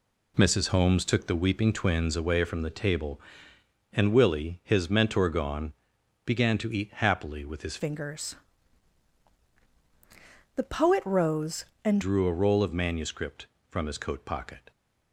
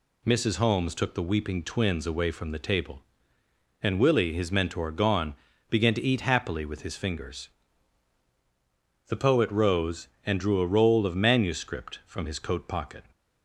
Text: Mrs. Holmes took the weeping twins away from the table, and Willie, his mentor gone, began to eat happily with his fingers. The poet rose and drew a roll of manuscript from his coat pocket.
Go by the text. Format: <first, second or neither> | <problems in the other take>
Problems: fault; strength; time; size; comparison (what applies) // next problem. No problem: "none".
second | changes voice from "fingers" to "and"; from 7.7 to 12.0 s; 4.3 s long